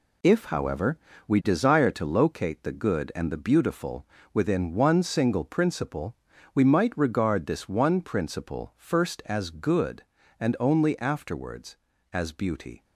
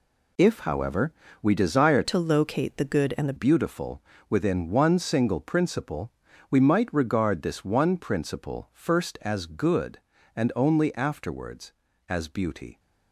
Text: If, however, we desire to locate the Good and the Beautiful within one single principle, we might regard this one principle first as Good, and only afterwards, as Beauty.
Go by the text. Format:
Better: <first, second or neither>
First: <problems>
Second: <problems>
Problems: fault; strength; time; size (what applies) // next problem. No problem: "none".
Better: first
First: pauses between "Beautiful" and "within"; slight; at 4.0 s; 0.28 s long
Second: changes voice from "to" to "the"; from 2.0 to 3.3 s; 1.3 s long // pauses between "Beautiful" and "within"; slight; at 4.0 s; 0.28 s long